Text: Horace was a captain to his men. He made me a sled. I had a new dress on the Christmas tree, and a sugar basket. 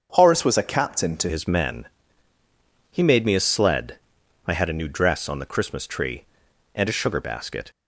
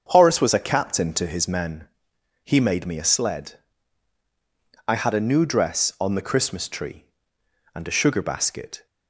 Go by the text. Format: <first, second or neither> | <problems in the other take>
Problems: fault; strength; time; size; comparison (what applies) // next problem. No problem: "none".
second | starts louder than the rest; strong; until 1.1 s; 7 dB; also in the second // changes voice at "his"; from 1.2 s on; 6.5 s long